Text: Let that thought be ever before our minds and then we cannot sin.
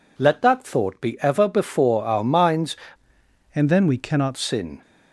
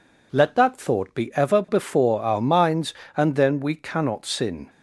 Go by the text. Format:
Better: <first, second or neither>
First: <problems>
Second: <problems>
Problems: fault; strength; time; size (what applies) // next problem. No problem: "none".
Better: second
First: changes voice from "and" to "cannot"; from 3.5 to 4.3 s; 0.8 s long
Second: none